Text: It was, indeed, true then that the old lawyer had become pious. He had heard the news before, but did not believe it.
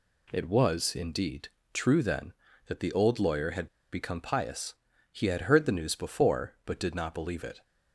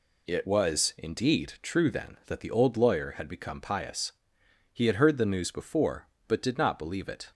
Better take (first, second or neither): second